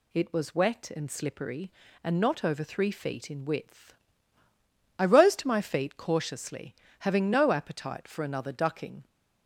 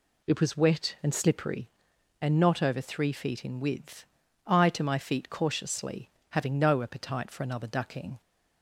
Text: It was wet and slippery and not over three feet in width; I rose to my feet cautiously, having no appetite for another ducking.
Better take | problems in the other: first | skips "rose"; at 4.6 s

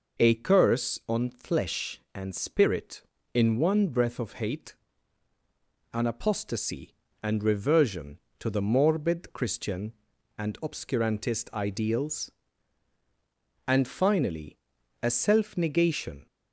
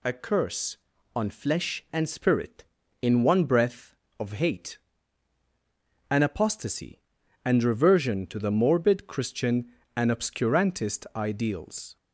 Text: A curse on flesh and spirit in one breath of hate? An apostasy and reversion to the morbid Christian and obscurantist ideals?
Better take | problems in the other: second | goes on to say "And finally a self negation"; strong; from 13.6 s on; 2.6 s long

